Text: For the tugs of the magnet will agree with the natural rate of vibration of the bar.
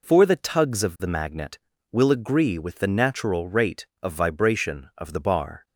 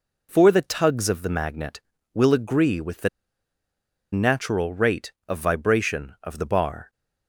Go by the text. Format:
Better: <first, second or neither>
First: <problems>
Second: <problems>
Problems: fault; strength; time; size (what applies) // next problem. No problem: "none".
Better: first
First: none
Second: pauses between "the" and "natural"; at 3.0 s; 1.0 s long